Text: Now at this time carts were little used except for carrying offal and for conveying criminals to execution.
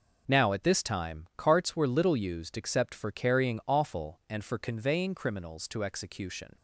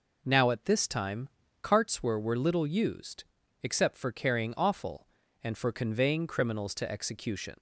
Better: first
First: none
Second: pauses between "time" and "carts"; slight; at 1.2 s; 0.34 s long // says "were" twice; at 2.1 s // pauses between "used" and "except"; at 3.2 s; 0.40 s long

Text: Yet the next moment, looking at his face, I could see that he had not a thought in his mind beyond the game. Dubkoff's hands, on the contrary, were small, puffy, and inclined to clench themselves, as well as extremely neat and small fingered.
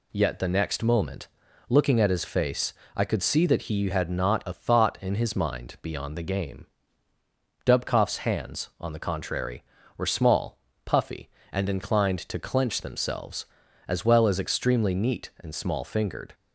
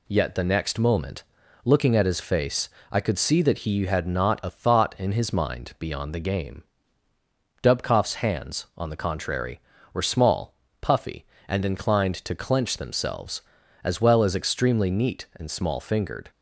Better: neither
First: none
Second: none

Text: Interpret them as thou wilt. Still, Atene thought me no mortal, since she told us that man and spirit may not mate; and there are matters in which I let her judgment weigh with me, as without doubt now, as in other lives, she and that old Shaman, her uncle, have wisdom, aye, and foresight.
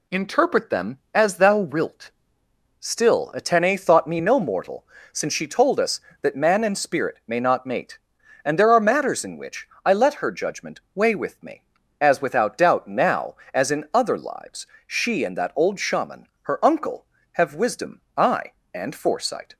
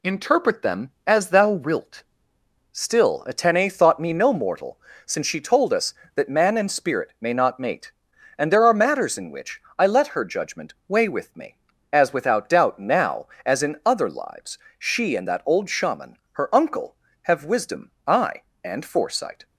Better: neither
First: pauses between "which" and "I"; slight; at 9.6 s; 0.16 s long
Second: pauses between "which" and "I"; slight; at 9.6 s; 0.16 s long

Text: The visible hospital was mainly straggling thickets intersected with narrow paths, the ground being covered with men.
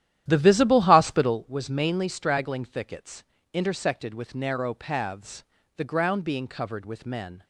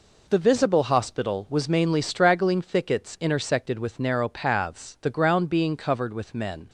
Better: second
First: starts louder than the rest; strong; until 1.3 s; 12 dB // pauses between "thickets" and "intersected"; slight; at 3.2 s; 0.30 s long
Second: none

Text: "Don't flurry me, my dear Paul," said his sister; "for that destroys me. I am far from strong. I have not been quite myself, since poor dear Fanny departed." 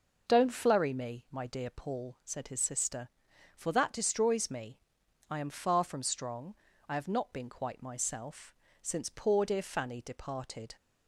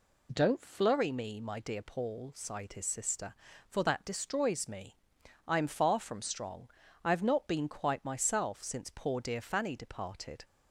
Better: first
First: none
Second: says "sighed" for "said"; at 2.3 s

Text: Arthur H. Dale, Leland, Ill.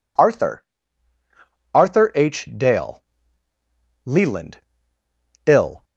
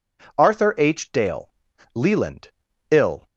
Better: second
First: says "Arthur" twice; at 1.7 s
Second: none

